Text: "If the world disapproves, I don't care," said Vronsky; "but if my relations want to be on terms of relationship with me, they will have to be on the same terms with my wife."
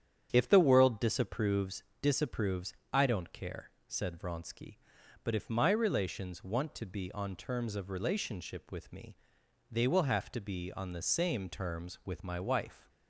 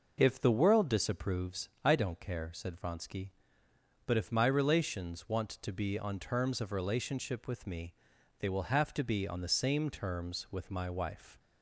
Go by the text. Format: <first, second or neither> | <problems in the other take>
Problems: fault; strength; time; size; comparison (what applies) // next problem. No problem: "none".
second | starts louder than the rest; strong; until 1.3 s; 9 dB // says "disapproves" twice; at 2.0 s